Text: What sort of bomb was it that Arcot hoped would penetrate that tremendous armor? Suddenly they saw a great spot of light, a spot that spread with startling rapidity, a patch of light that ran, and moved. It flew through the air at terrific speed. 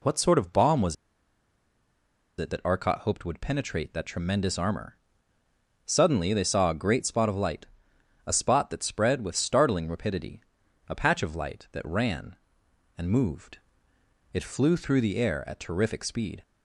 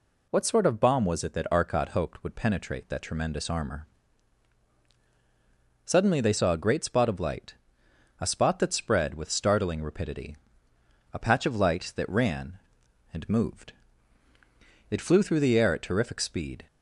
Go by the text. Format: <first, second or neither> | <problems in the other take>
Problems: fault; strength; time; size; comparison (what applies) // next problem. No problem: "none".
second | pauses between "was" and "it"; strong; at 0.9 s; 1.4 s long